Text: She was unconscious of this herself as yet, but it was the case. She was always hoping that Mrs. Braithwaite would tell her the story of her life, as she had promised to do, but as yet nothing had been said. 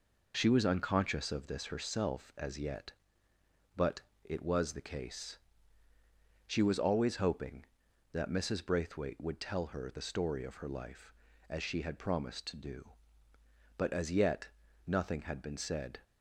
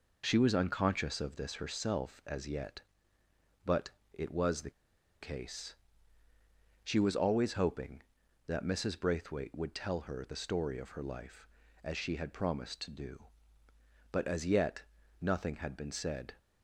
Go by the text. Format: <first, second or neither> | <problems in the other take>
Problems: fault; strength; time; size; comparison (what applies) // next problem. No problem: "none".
first | pauses between "but" and "it"; slight; at 3.9 s; 0.24 s long; slight in the first // pauses between "the" and "case"; noticeable; at 4.7 s; 0.50 s long // pauses between "yet" and "nothing"; slight; at 14.8 s; 0.36 s long; slight in the first